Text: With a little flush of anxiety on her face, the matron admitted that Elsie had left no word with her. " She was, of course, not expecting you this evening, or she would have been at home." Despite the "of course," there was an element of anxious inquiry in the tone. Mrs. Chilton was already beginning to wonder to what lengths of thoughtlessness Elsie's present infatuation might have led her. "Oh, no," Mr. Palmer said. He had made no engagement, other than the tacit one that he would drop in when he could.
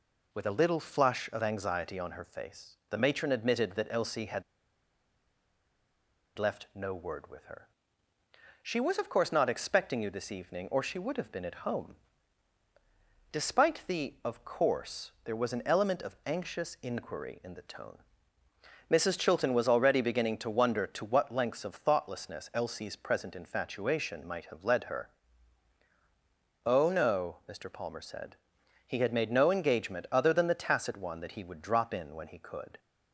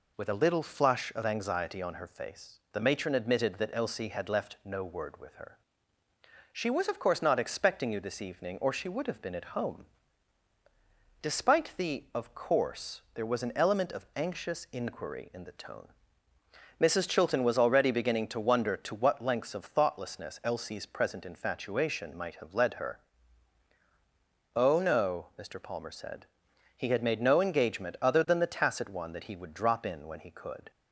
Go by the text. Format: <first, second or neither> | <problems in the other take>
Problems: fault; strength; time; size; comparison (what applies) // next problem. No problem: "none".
second | pauses between "had" and "left"; strong; at 4.4 s; 1.9 s long